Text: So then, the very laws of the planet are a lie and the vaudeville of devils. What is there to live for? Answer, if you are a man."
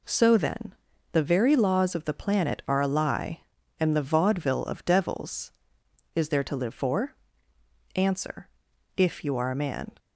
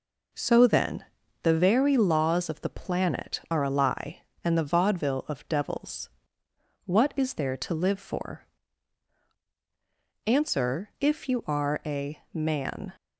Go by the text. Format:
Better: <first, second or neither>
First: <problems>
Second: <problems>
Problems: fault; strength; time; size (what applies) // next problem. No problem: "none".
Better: second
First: skips "What"; at 5.8 s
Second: none